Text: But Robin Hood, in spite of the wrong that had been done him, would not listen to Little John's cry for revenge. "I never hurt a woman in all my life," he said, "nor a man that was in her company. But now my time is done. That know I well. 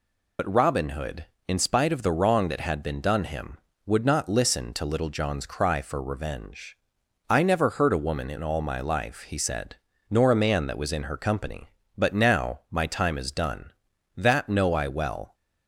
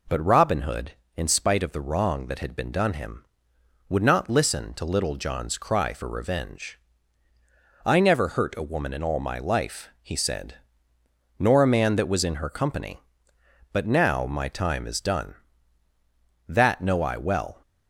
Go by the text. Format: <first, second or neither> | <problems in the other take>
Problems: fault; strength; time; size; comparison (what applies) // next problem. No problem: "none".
second | loses the start of "But"; at 0.3 s; 80 ms